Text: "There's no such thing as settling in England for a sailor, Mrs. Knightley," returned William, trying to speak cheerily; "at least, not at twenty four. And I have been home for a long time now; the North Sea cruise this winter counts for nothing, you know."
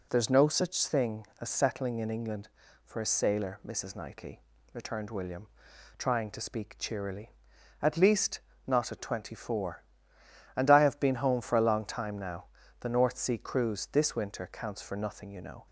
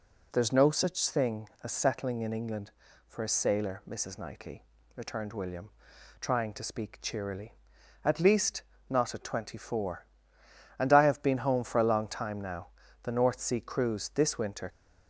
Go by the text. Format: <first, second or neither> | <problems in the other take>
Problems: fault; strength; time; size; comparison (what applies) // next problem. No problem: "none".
first | stops before "counts for nothing you know"; at 14.6 s